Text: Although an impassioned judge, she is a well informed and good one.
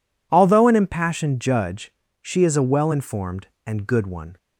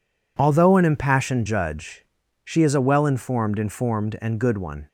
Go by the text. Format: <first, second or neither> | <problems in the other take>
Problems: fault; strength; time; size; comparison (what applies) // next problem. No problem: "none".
first | says "informed" twice; at 3.5 s